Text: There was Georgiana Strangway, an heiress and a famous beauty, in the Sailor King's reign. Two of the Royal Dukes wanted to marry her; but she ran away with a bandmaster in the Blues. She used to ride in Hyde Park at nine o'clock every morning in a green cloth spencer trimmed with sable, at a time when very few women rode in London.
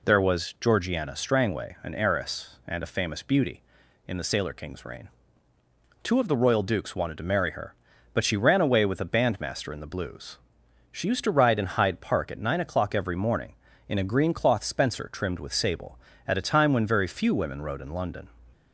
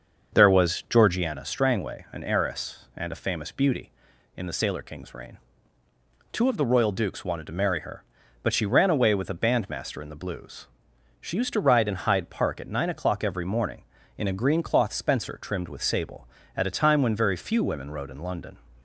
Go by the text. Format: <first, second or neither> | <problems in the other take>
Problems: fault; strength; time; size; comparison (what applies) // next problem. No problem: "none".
first | starts louder than the rest; until 1.3 s; 6.5 dB